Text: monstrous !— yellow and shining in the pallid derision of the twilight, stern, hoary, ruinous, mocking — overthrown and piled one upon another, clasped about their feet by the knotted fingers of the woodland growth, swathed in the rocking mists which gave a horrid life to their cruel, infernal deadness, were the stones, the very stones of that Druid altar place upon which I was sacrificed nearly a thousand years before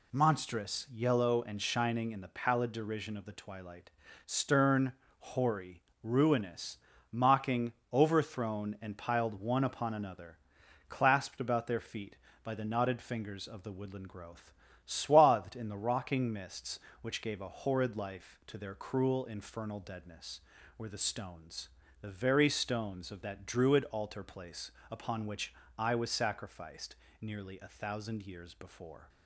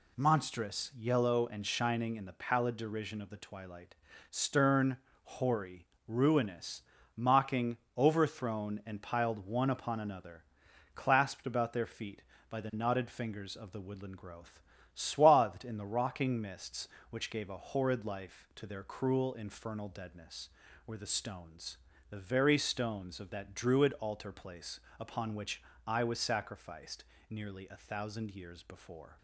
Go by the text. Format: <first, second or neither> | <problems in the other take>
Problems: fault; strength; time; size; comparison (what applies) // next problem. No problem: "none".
neither | pauses between "place" and "upon"; slight; the same in both // pauses between "which" and "I"; slight; the same in both // pauses between "sacrificed" and "nearly"; slight; the same in both